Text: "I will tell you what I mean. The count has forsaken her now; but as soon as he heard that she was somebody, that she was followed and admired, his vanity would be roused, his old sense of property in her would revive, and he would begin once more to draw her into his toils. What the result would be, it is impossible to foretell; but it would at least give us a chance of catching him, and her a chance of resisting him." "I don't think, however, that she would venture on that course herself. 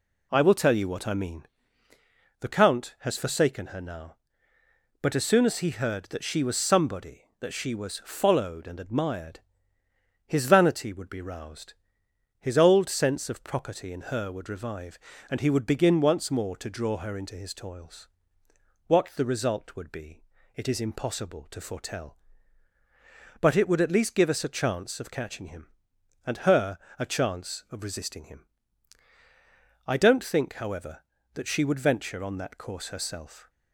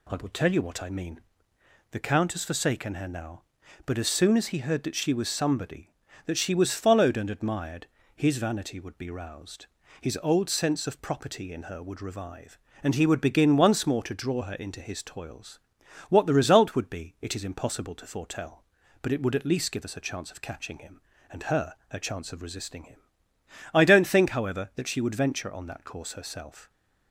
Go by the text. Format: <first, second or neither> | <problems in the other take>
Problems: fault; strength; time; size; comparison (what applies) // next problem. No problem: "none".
neither | pauses between "her" and "a"; slight; the same in both